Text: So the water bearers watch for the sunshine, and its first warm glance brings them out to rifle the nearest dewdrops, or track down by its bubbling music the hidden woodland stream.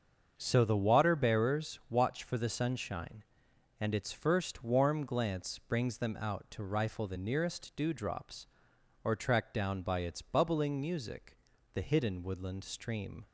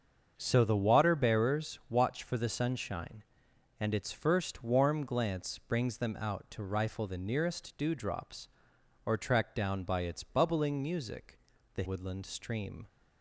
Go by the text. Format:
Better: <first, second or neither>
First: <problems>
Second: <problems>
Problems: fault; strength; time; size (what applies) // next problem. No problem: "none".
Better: first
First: starts louder than the rest; until 1.3 s; 7 dB // pauses between "music" and "the"; at 11.3 s; 0.38 s long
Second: starts louder than the rest; until 1.3 s; 7 dB // pauses between "music" and "the"; at 11.3 s; 0.38 s long // skips "hidden"; at 11.8 s